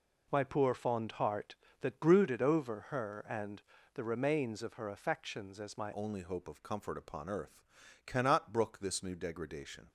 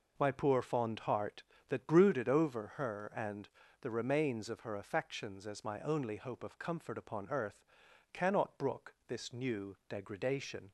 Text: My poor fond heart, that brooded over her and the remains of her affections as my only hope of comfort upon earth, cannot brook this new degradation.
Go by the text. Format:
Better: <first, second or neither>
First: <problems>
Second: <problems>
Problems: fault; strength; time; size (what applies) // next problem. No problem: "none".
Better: second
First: pauses between "and" and "the"; slight; at 3.6 s; 0.32 s long // changes voice at "only"; from 5.9 s on; 3.9 s long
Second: pauses between "and" and "the"; slight; at 3.4 s; 0.32 s long